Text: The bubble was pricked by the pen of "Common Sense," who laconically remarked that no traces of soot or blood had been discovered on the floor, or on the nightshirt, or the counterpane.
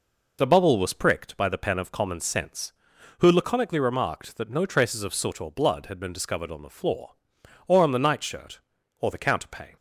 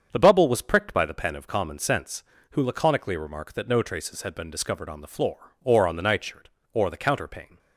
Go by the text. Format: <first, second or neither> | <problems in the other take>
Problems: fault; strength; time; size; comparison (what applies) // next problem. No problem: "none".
first | starts louder than the rest; strong; until 1.1 s; 7.5 dB // skips "of soot or blood"; at 4.2 s